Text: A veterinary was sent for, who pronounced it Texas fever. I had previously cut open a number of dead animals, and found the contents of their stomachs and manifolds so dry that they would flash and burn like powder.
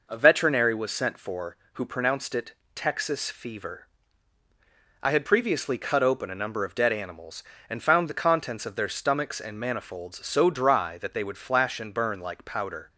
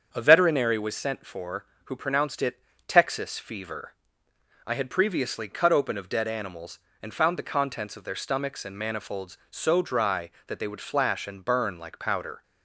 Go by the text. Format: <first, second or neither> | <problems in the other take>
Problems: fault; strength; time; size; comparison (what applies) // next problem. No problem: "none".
first | starts louder than the rest; strong; until 1.1 s; 7.5 dB // pauses between "it" and "Texas"; slight; at 2.5 s; 0.30 s long; slight in the first // skips "a number"; at 5.9 s